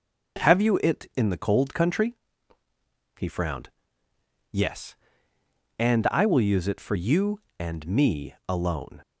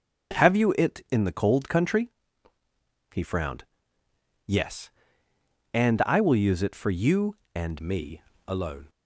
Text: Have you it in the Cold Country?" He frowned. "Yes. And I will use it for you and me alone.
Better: first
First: none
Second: starts louder than the rest; strong; until 1.4 s; 7.5 dB // changes voice at "me"; from 7.8 s on; 1.0 s long // pauses between "me" and "alone"; slight; at 8.2 s; 0.26 s long

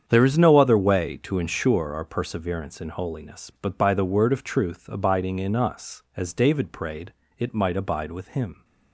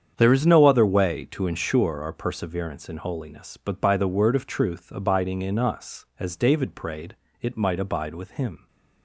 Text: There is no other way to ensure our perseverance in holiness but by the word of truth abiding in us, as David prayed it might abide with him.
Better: neither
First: starts louder than the rest; strong; until 1.0 s; 8 dB // pauses between "prayed" and "it"; slight; at 7.1 s; 0.26 s long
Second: starts louder than the rest; strong; until 1.1 s; 8 dB // pauses between "prayed" and "it"; slight; at 7.1 s; 0.26 s long

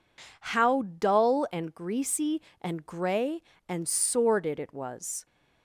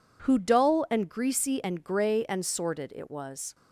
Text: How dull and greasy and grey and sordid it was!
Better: first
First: none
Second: says "Who" for "How"; at 0.2 s

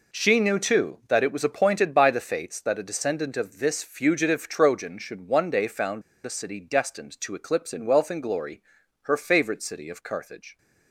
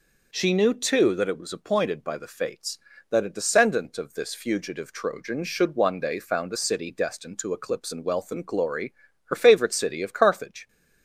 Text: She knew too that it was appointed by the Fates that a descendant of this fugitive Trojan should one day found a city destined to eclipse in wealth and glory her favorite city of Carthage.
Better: second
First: pauses between "found" and "a"; slight; at 6.0 s; 0.23 s long // pauses between "glory" and "her"; at 8.6 s; 0.38 s long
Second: pauses between "glory" and "her"; slight; at 8.9 s; 0.32 s long

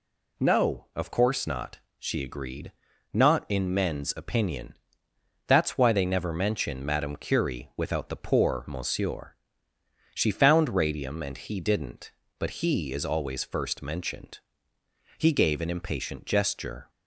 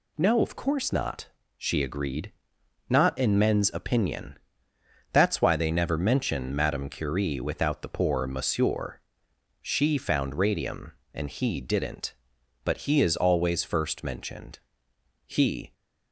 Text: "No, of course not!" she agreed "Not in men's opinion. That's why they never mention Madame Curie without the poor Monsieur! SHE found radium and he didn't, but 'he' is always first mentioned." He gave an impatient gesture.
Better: first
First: pauses between "agreed" and "Not"; at 2.7 s; 0.42 s long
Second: pauses between "agreed" and "Not"; noticeable; at 2.3 s; 0.54 s long // stops before "gave an impatient gesture"; at 15.7 s

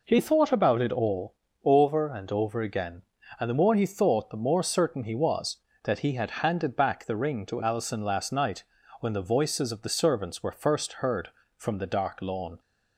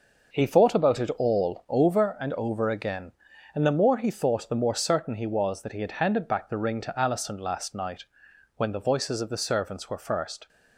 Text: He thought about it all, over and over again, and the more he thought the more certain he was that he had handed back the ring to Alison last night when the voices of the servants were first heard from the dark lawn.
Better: first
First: pauses between "night" and "when"; slight; at 8.6 s; 0.36 s long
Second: pauses between "night" and "when"; noticeable; at 8.0 s; 0.52 s long // stops before "heard from the dark lawn"; at 10.4 s

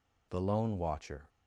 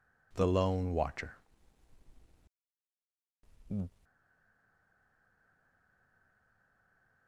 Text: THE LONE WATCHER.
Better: first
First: none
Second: stays silent after the last word; strong; from 4.0 s on; 3.2 s long

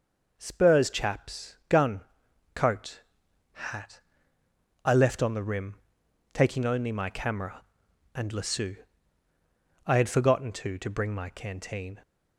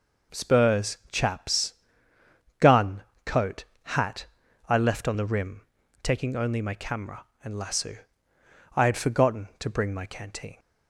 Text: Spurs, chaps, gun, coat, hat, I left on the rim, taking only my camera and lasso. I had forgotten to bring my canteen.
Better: second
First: says "to" twice; at 10.7 s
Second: none

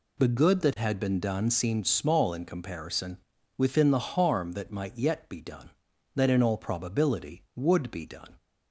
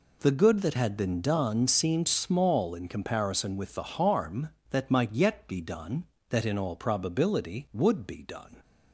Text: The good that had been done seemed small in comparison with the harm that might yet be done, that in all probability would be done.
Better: second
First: says "within" for "with"; at 3.5 s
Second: none

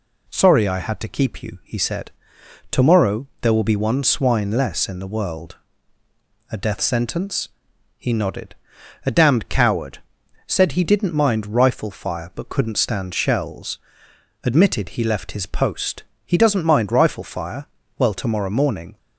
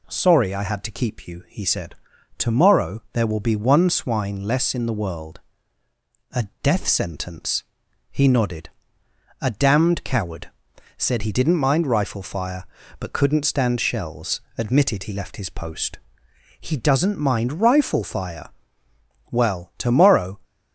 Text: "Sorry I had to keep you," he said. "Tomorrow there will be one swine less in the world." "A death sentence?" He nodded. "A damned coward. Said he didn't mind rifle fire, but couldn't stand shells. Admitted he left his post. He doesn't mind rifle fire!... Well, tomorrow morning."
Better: first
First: none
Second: stops before "morning"; at 20.4 s

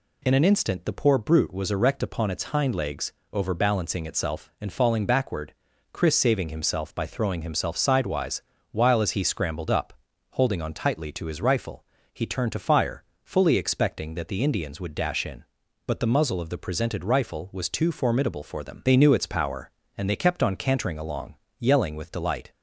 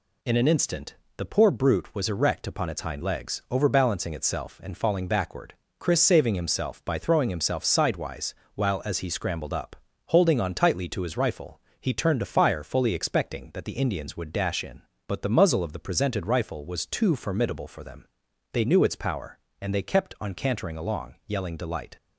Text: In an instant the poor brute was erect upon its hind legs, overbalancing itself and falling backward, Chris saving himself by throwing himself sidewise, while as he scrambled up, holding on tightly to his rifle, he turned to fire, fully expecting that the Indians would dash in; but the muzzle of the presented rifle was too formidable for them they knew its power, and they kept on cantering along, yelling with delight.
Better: first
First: none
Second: pauses between "instant" and "the"; slight; at 0.9 s; 0.24 s long // pauses between "them" and "they"; noticeable; at 18.0 s; 0.48 s long // skips "with"; at 21.5 s

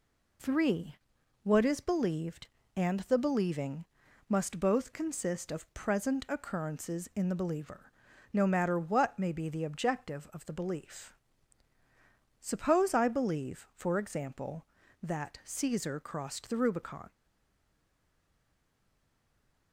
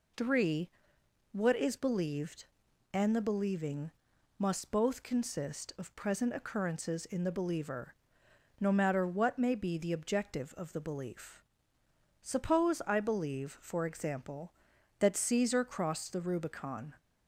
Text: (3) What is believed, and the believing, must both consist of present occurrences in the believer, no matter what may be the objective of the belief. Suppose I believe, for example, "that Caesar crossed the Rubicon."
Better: second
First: stays silent after the last word; strong; from 17.1 s on; 2.6 s long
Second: none

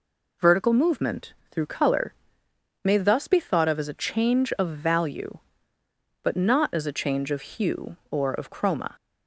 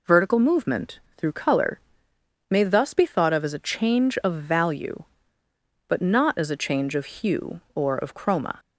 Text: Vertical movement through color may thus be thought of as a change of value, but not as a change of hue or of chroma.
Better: neither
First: pauses between "movement" and "through"; slight; at 1.3 s; 0.18 s long // pauses between "color" and "may"; noticeable; at 2.1 s; 0.72 s long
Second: pauses between "movement" and "through"; slight; at 0.9 s; 0.18 s long // pauses between "color" and "may"; noticeable; at 1.7 s; 0.72 s long

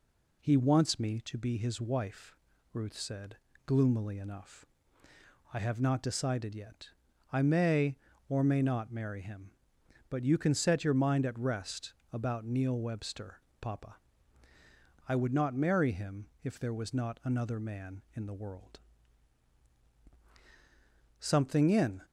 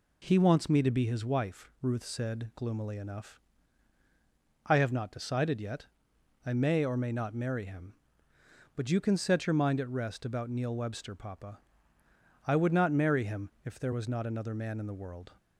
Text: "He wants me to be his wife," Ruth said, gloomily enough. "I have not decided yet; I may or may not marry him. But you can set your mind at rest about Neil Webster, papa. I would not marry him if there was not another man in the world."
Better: second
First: pauses between "rest" and "about"; slight; at 11.9 s; 0.20 s long // pauses between "him" and "if"; slight; at 16.2 s; 0.16 s long // goes on to say "Something in"; noticeable; from 21.1 s on; 0.84 s long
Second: pauses between "him" and "if"; slight; at 13.4 s; 0.16 s long

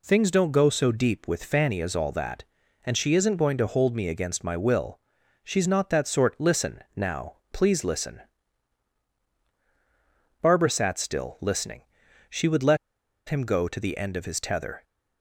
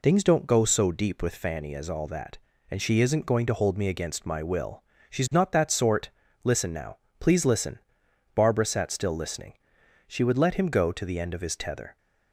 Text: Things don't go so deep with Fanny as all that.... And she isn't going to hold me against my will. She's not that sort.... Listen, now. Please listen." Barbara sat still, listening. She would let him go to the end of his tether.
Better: second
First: pauses between "let" and "him"; noticeable; at 12.7 s; 0.52 s long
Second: none

